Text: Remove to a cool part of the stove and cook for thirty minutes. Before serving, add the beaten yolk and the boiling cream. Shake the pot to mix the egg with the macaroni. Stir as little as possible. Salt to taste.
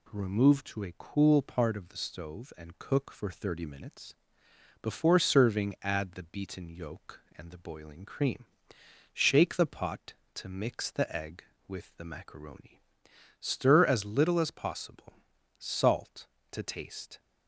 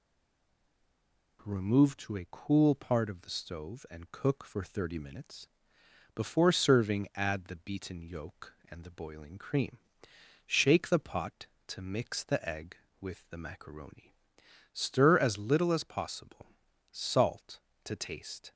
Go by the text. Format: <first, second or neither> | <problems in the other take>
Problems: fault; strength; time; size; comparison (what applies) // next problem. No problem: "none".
first | stays silent before the first word; noticeable; until 1.3 s; 1.3 s long